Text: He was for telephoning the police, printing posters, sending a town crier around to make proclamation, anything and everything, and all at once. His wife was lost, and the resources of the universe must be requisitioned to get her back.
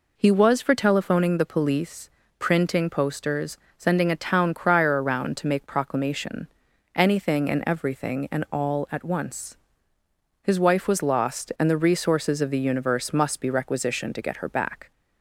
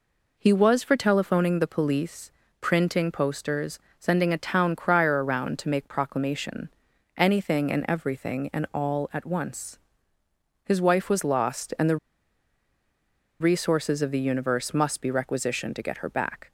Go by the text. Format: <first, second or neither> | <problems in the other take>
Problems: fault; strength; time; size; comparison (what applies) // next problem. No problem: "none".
first | pauses between "the" and "resources"; strong; at 11.9 s; 1.4 s long